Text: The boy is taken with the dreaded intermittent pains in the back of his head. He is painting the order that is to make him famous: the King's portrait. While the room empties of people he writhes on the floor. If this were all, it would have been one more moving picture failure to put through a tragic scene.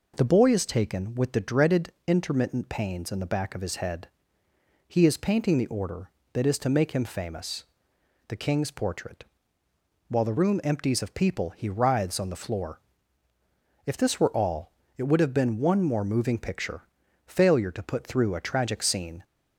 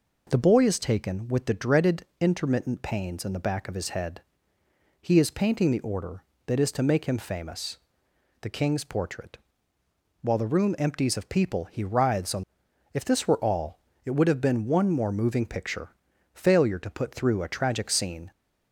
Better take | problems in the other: first | pauses between "dreaded" and "intermittent"; slight; at 2.0 s; 0.16 s long; slight in the first // skips "the floor"; at 12.6 s // pauses between "picture" and "failure"; at 15.9 s; 0.42 s long; also in the first

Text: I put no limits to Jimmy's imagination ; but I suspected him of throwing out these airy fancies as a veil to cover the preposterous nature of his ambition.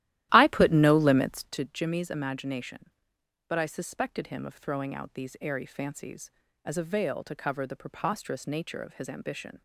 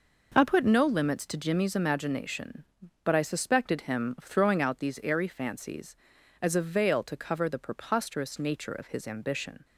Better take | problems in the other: second | starts louder than the rest; strong; until 1.7 s; 14 dB

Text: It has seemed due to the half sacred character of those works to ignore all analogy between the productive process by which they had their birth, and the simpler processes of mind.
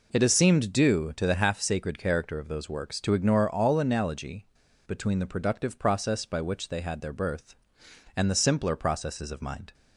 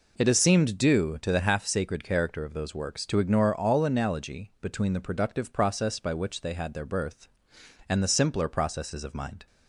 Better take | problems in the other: second | pauses between "analogy" and "between"; at 4.4 s; 0.41 s long

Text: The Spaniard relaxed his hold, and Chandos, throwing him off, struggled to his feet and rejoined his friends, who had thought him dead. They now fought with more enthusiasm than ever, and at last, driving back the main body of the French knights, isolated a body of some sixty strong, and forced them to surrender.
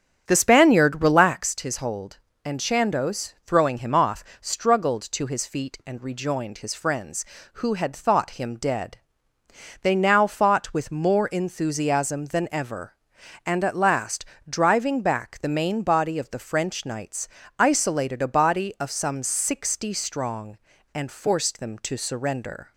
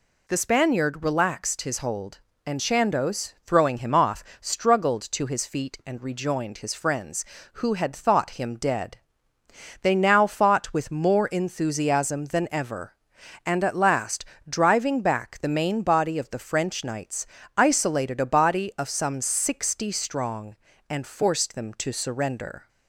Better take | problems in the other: second | starts louder than the rest; strong; until 1.5 s; 8 dB

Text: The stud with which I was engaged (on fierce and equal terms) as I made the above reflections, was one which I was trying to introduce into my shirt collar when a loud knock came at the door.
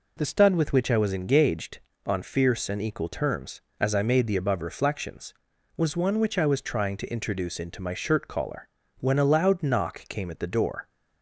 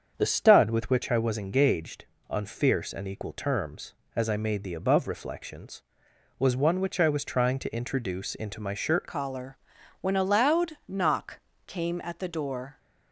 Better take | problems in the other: first | starts louder than the rest; until 1.1 s; 7 dB // changes voice at "collar"; from 9.0 s on; 3.7 s long // pauses between "collar" and "when"; at 9.5 s; 0.44 s long; slight in the first // pauses between "knock" and "came"; slight; at 11.3 s; 0.30 s long

